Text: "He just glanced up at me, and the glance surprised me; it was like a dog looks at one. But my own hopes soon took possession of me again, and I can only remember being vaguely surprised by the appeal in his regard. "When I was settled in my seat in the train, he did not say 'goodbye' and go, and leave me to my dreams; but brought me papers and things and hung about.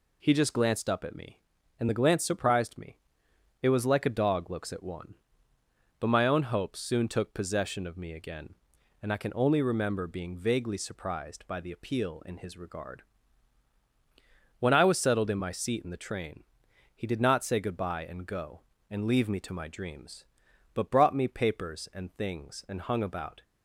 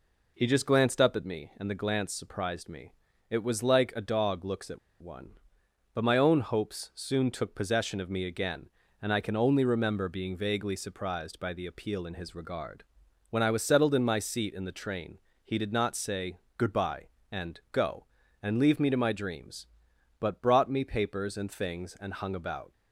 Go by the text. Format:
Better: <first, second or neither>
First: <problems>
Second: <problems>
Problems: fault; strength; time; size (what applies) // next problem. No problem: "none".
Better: first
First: none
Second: pauses between "at" and "one"; slight; at 4.7 s; 0.23 s long // pauses between "say" and "goodbye"; slight; at 16.3 s; 0.18 s long